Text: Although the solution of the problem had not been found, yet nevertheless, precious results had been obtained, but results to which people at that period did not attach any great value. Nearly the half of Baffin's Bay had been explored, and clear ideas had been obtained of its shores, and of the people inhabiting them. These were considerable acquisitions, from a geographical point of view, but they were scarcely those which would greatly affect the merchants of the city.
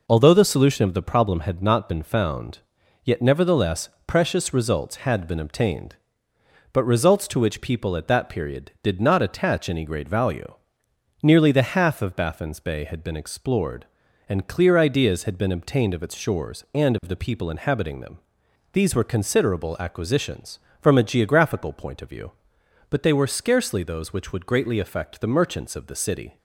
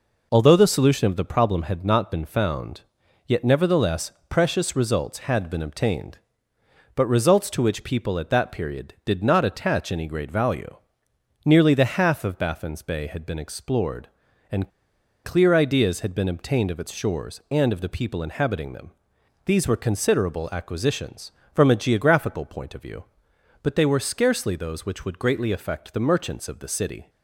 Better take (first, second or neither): first